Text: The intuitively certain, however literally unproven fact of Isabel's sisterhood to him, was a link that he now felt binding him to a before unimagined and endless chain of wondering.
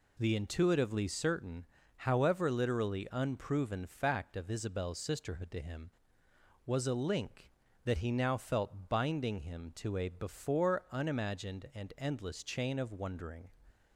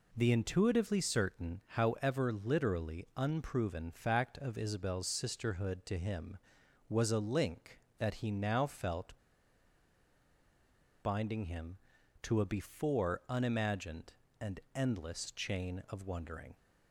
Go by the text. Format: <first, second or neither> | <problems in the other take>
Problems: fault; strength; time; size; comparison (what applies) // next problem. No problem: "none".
first | pauses between "felt" and "binding"; strong; at 9.1 s; 1.8 s long // pauses between "and" and "endless"; slight; at 14.5 s; 0.16 s long